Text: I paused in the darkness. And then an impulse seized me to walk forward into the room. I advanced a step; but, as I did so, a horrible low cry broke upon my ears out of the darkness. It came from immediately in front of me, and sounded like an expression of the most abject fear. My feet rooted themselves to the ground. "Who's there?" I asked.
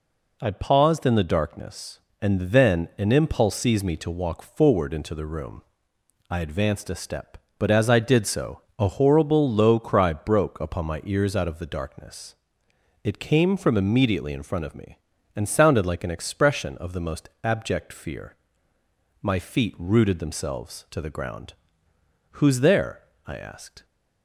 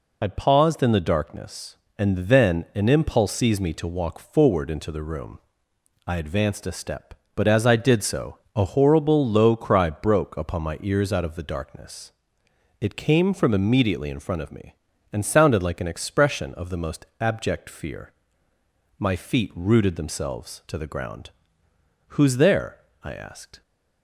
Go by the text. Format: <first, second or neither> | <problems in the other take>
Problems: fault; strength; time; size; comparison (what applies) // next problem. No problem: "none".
first | loses the start of "I"; at 0.2 s; 40 ms // pauses between "most" and "abject"; slight; at 17.0 s; 0.16 s long; slight in the first